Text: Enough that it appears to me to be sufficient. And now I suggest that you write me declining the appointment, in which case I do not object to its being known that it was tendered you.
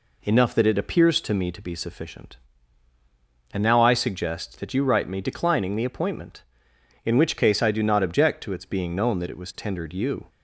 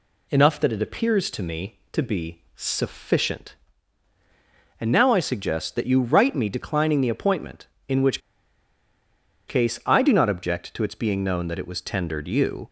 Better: first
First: none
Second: pauses between "which" and "case"; strong; at 8.2 s; 1.2 s long

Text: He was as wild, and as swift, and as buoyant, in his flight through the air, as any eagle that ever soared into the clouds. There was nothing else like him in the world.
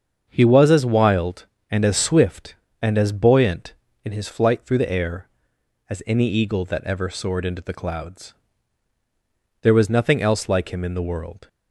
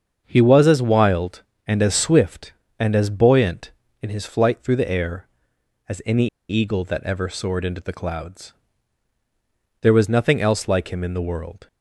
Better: first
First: starts louder than the rest; until 1.2 s; 7 dB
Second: starts louder than the rest; until 1.2 s; 7 dB // pauses between "any" and "eagle"; slight; at 6.2 s; 0.22 s long

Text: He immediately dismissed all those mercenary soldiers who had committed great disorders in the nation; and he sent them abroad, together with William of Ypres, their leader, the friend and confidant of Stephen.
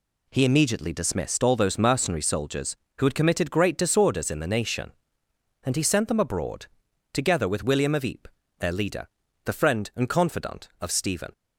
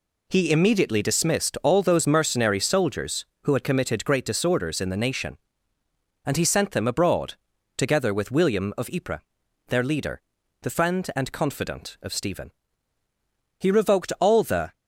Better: first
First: none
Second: goes on to say "He revoked all the"; noticeable; from 13.5 s on; 1.1 s long

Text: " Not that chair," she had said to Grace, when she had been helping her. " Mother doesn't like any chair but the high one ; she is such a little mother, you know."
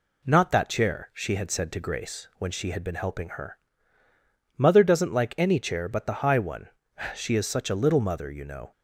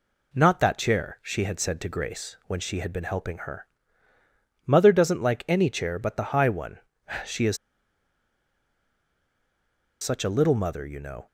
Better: first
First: none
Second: pauses between "is" and "such"; strong; at 7.5 s; 2.4 s long

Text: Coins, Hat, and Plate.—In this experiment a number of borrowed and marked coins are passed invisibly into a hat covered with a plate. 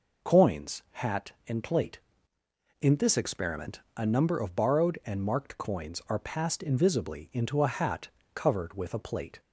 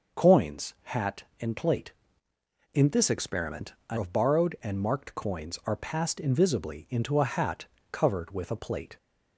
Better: first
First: pauses between "experiment" and "a"; slight; at 3.7 s; 0.16 s long // pauses between "hat" and "covered"; slight; at 8.0 s; 0.26 s long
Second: pauses between "experiment" and "a"; slight; at 3.7 s; 0.16 s long // skips "number"; at 3.9 s // pauses between "hat" and "covered"; slight; at 7.6 s; 0.26 s long

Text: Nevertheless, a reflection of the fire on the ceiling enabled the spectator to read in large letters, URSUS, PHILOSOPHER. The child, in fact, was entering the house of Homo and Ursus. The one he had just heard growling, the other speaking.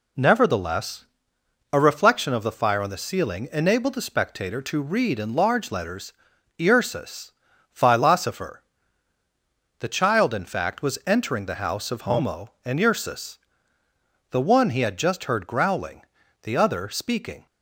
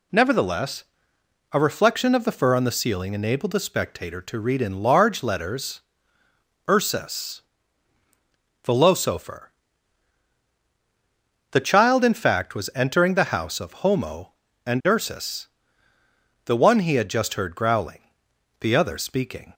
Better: first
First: none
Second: says "fur" for "fire"; at 2.3 s

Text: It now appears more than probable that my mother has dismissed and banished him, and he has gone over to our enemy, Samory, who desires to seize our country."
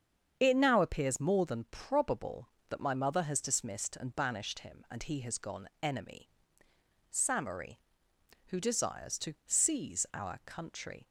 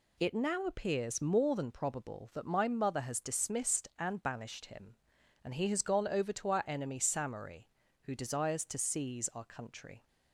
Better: second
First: starts louder than the rest; strong; until 1.3 s; 7.5 dB // skips "over to our"; at 5.7 s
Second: none

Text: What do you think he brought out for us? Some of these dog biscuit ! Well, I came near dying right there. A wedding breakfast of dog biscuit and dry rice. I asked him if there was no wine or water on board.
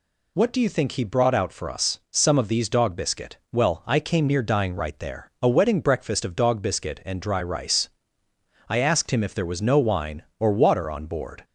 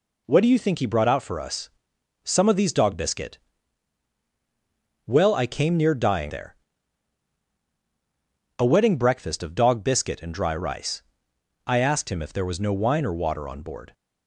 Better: first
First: none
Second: skips "right"; at 6.3 s

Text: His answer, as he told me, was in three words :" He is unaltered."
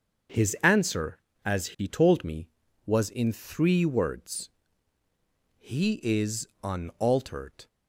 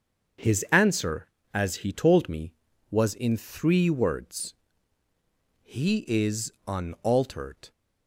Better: neither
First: starts louder than the rest; strong; until 1.6 s; 8 dB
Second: starts louder than the rest; strong; until 1.7 s; 7.5 dB

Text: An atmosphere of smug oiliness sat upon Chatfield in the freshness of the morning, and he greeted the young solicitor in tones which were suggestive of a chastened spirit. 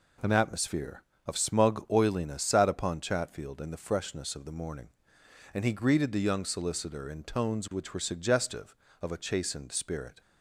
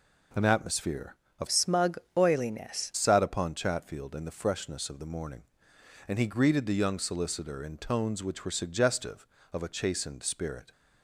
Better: first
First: none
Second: changes voice from "smug" to "oiliness"; from 1.4 to 2.9 s; 1.5 s long // pauses between "smug" and "oiliness"; slight; at 1.9 s; 0.18 s long

